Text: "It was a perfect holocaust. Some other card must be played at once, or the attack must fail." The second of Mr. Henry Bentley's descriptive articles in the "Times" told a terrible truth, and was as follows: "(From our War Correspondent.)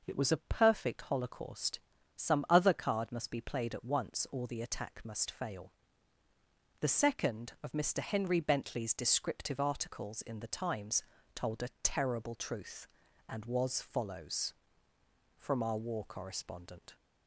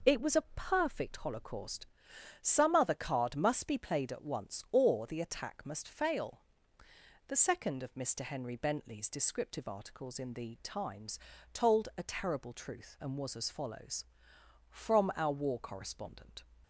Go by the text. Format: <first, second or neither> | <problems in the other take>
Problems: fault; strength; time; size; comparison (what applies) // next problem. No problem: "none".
second | pauses between "Times" and "told"; slight; at 11.0 s; 0.32 s long; slight in the second // skips "as"; at 13.7 s